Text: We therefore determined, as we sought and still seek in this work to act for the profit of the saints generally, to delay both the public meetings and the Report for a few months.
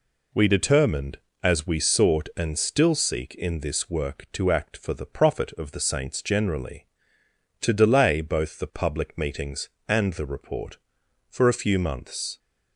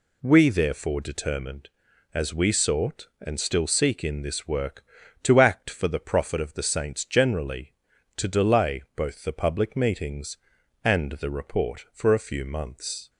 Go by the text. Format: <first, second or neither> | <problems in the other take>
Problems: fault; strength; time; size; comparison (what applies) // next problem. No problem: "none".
second | skips "therefore"; at 0.4 s